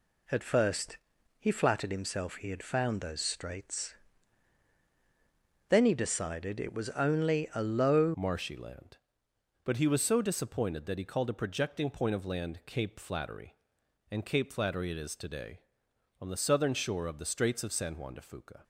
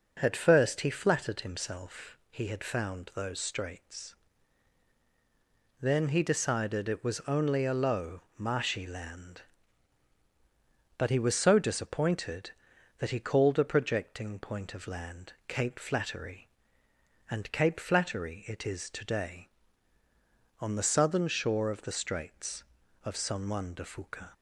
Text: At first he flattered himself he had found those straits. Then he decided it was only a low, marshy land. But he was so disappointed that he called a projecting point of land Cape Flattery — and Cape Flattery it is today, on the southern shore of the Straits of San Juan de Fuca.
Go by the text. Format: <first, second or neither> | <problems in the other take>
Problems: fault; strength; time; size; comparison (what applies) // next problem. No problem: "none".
second | pauses between "first" and "he"; at 0.9 s; 0.42 s long // changes voice at "marshy"; from 8.1 s on; 10.5 s long